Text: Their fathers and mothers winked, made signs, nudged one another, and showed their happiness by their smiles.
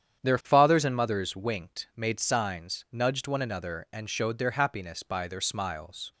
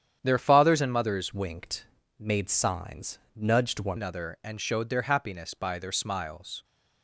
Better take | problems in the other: first | starts louder than the rest; strong; until 1.2 s; 9 dB; strong in the first // changes voice from "winked" to "one"; from 1.3 to 3.9 s; 2.6 s long

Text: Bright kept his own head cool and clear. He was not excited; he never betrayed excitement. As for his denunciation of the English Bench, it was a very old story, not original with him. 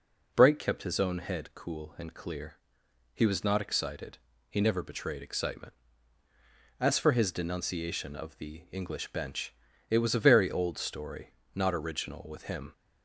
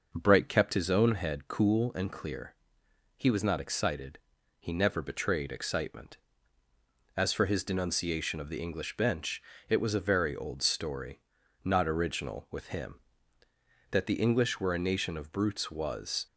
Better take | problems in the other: first | goes on to say "That the English were a nation of brutes was"; strong; from 13.9 s on; 2.3 s long

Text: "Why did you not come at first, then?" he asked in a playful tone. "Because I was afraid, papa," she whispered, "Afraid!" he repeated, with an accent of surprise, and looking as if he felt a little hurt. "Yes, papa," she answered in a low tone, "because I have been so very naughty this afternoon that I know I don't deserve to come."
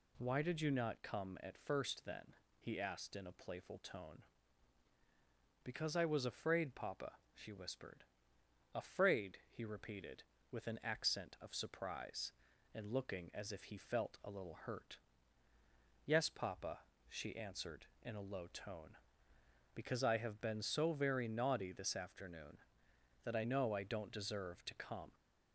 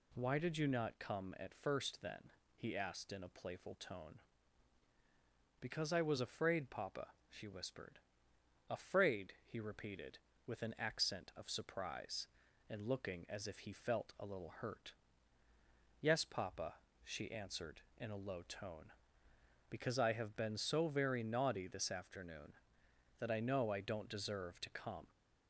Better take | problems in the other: neither | none

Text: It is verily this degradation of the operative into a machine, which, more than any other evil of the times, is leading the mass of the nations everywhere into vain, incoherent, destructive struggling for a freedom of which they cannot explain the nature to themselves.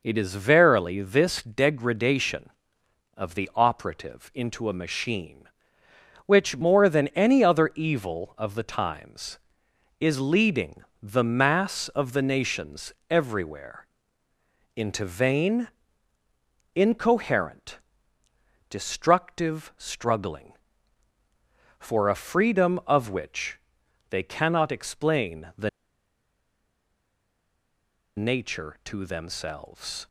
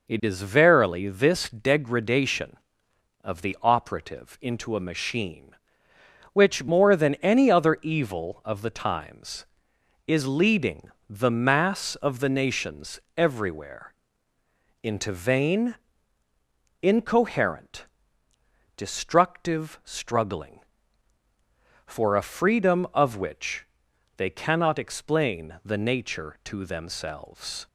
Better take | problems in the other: second | pauses between "leading" and "the"; slight; at 10.8 s; 0.20 s long; slight in the second // pauses between "nations" and "everywhere"; slight; at 12.9 s; 0.18 s long; slight in the second // pauses between "everywhere" and "into"; noticeable; at 13.8 s; 0.90 s long; noticeable in the second // pauses between "which" and "they"; noticeable; at 23.5 s; 0.52 s long; noticeable in the second // pauses between "the" and "nature"; strong; at 25.6 s; 2.4 s long

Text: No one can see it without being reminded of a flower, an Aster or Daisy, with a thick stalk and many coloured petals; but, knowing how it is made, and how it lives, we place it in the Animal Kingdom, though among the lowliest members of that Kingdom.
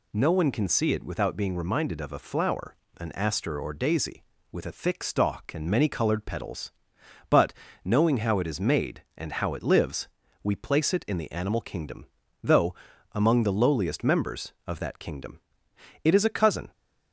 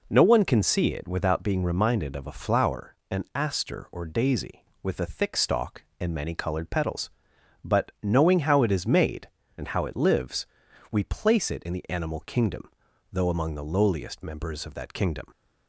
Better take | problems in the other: second | pauses between "though" and "among"; at 12.7 s; 0.38 s long // goes on to say "It is a cousin"; noticeable; from 16.0 s on; 0.66 s long

